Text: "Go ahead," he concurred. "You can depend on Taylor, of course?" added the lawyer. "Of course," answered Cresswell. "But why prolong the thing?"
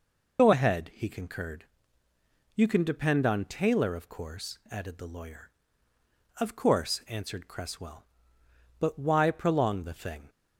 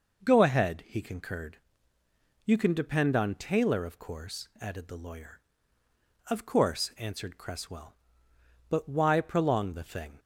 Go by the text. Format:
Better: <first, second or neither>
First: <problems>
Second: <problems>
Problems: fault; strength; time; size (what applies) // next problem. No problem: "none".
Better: second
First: loses the start of "Go"; at 0.3 s; 90 ms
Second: none